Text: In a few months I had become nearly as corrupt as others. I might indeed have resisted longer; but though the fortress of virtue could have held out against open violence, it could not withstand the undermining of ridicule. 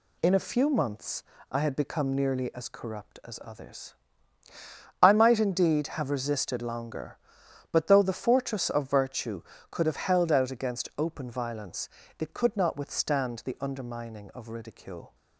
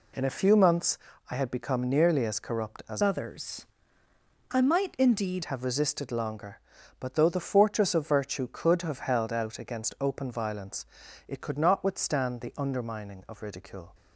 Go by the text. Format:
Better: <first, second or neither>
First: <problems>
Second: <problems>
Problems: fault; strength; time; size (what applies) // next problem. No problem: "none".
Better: first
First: pauses between "months" and "I"; slight; at 1.2 s; 0.28 s long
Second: pauses between "months" and "I"; slight; at 0.9 s; 0.32 s long // changes voice from "others" to "indeed"; from 3.0 to 5.4 s; 2.4 s long